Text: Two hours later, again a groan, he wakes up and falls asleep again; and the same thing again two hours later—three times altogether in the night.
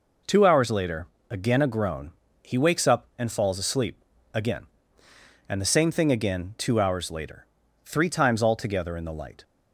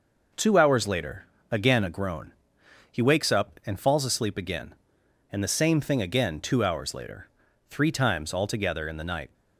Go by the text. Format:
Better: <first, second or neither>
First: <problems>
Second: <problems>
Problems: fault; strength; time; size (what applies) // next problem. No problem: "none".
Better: second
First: pauses between "asleep" and "again"; slight; at 3.9 s; 0.36 s long // says "light" for "night"; at 9.1 s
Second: none